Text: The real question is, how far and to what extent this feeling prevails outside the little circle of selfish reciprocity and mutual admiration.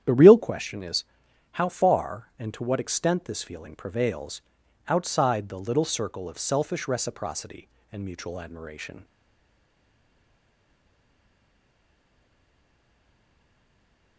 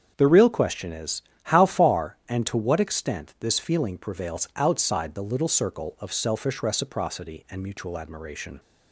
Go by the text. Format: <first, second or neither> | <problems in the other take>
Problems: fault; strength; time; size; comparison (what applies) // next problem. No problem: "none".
second | starts louder than the rest; strong; until 1.0 s; 10 dB; strong in the second // pauses between "prevails" and "outside"; noticeable; at 4.4 s; 0.48 s long // stays silent after the last word; strong; from 9.0 s on; 5.1 s long